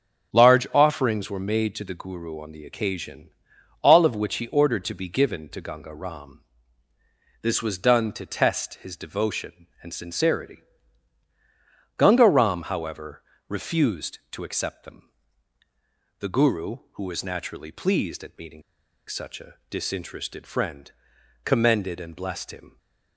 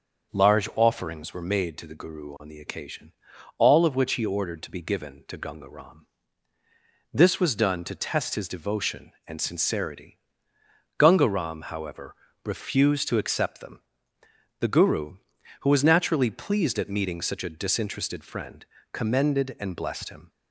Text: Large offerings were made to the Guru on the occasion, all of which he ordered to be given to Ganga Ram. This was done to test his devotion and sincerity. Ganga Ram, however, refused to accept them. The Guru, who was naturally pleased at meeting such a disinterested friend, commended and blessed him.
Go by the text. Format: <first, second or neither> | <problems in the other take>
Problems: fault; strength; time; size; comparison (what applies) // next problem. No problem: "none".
second | starts louder than the rest; until 1.3 s; 6.5 dB; also in the second // pauses between "meeting" and "such"; at 18.6 s; 0.45 s long // pauses between "a" and "disinterested"; slight; at 19.5 s; 0.16 s long